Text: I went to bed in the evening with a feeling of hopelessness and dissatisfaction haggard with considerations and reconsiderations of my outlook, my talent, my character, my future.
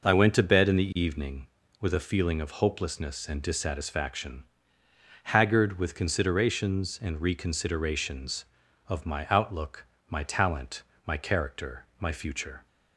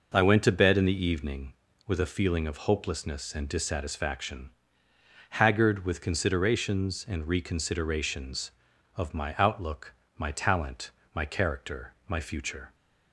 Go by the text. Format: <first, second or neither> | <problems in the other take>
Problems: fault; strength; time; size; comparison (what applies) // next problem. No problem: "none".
neither | pauses between "dissatisfaction" and "haggard"; noticeable; the same in both